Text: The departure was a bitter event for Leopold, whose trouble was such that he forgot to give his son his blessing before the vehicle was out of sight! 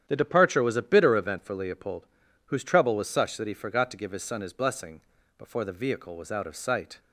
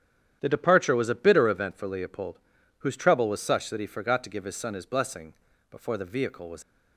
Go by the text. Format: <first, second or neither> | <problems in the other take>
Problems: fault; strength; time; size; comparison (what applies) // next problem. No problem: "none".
first | starts louder than the rest; strong; until 1.4 s; 9.5 dB; strong in the first // pauses between "blessing" and "before"; slight; at 5.3 s; 0.36 s long; slight in the first // stops before "out of sight"; at 6.6 s